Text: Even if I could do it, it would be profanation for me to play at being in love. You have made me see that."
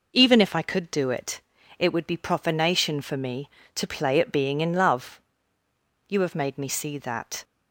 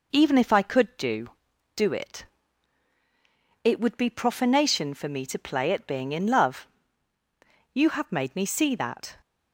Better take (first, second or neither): first